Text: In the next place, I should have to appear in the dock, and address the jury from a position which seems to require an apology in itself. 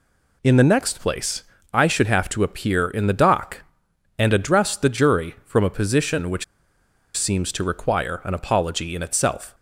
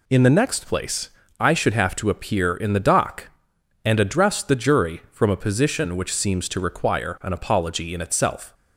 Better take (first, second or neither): second